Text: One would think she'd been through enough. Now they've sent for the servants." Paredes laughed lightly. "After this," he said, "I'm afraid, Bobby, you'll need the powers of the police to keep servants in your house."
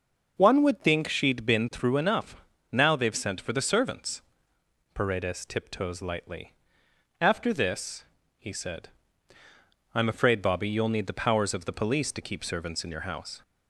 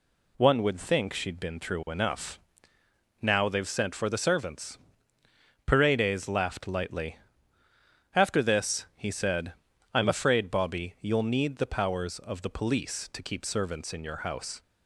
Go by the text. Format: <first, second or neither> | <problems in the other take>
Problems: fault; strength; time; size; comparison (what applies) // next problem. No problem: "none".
second | says "tiptoes" for "laughed"; at 5.4 s